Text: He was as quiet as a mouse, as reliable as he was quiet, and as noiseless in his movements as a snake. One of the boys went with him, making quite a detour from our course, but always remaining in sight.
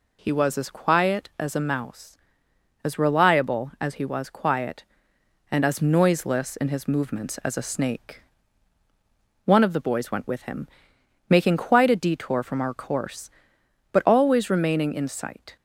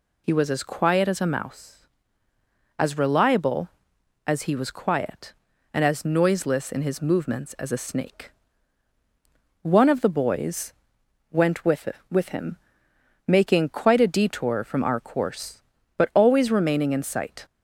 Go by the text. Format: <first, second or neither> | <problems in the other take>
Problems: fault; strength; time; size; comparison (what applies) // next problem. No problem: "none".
first | pauses between "boys" and "went"; noticeable; at 10.7 s; 0.58 s long // says "with" twice; at 12.1 s